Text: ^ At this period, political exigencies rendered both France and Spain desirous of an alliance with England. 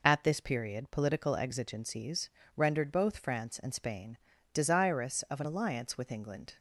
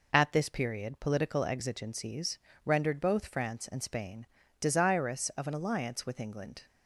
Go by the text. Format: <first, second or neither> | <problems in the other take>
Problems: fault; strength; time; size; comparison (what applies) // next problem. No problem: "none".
neither | pauses between "exigencies" and "rendered"; slight; the same in both // pauses between "Spain" and "desirous"; slight; the same in both